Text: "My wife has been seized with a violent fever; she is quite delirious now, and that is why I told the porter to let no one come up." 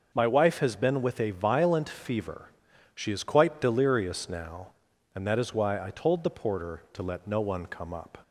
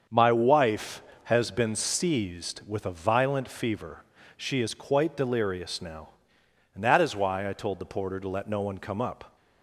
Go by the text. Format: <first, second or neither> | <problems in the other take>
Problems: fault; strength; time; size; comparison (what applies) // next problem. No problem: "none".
second | starts louder than the rest; noticeable; until 1.1 s; 6 dB; also in the second // skips "seized"; at 1.0 s